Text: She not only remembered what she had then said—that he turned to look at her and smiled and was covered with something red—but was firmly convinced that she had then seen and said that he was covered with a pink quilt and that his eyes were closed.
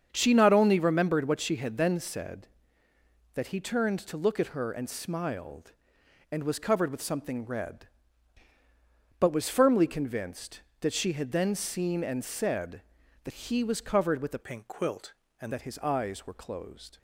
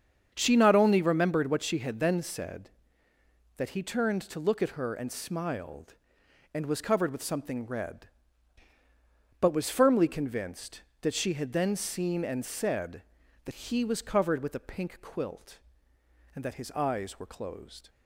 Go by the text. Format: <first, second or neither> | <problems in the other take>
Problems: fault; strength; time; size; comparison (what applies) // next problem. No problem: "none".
second | starts louder than the rest; strong; until 1.1 s; 7 dB; also in the second // changes voice from "pink" to "and"; from 14.4 to 15.5 s; 1.1 s long